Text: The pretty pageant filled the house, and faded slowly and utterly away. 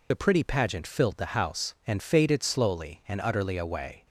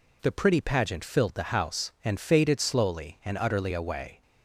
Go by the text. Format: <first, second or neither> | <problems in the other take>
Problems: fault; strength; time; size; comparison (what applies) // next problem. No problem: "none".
second | loses the start of "The"; at 0.1 s; 45 ms